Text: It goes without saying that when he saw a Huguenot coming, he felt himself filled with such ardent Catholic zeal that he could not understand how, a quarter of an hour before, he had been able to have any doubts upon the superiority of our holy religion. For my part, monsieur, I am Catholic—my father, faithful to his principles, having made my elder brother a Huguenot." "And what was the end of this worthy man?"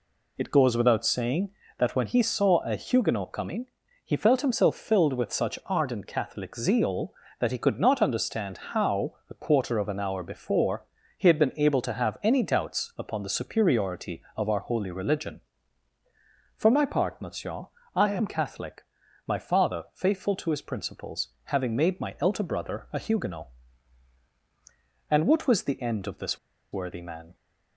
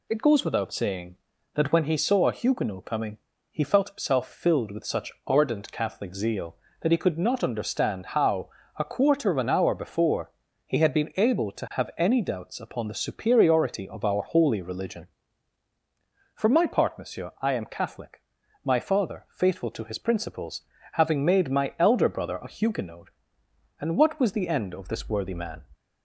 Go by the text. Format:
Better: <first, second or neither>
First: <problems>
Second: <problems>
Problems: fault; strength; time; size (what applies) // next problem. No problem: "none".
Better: second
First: pauses between "this" and "worthy"; slight; at 26.3 s; 0.34 s long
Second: none